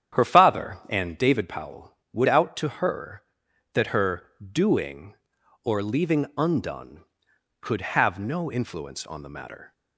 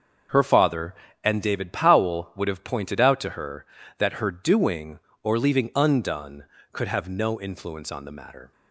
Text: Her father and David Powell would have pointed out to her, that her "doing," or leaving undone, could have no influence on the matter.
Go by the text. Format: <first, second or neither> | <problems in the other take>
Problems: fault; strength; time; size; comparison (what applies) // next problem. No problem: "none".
second | starts louder than the rest; strong; until 1.2 s; 9 dB; also in the second // skips "have pointed"; at 2.2 s // pauses between "her" and "doing"; slight; at 4.2 s; 0.24 s long